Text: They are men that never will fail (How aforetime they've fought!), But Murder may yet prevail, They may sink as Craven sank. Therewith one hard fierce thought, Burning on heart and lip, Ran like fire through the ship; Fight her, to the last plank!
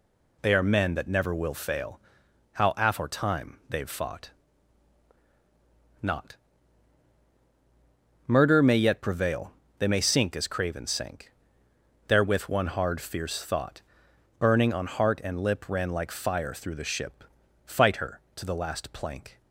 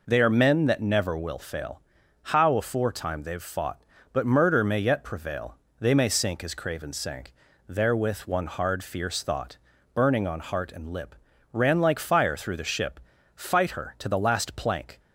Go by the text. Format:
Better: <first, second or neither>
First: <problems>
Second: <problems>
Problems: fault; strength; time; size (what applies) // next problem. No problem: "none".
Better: second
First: says "Not" for "But"; at 6.0 s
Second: none